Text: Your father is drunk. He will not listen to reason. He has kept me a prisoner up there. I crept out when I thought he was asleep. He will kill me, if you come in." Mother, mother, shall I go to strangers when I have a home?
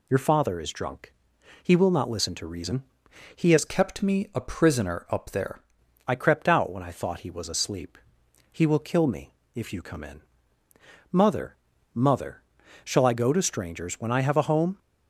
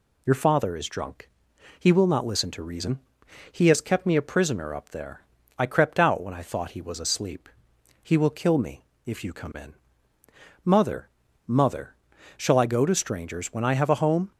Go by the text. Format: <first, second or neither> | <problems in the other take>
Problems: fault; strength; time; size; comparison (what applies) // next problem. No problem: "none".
second | changes voice from "kept" to "there"; from 3.6 to 5.6 s; 2.0 s long